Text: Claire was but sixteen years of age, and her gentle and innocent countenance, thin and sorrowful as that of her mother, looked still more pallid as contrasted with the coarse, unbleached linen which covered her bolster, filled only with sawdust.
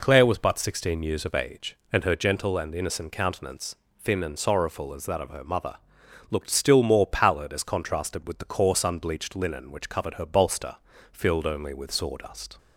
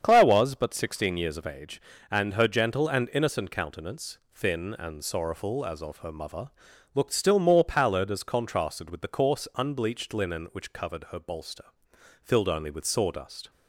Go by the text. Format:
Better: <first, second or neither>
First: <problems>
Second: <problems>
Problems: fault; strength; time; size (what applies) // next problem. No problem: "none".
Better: first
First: none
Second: starts louder than the rest; strong; until 1.0 s; 7.5 dB // skips "that"; at 5.7 s